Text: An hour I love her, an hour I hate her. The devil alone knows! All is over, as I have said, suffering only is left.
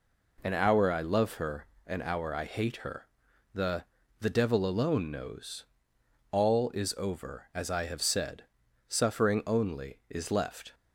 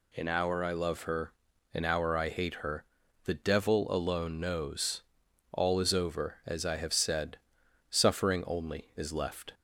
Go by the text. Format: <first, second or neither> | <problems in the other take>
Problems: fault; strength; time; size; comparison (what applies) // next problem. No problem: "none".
second | says "The" twice; at 4.2 s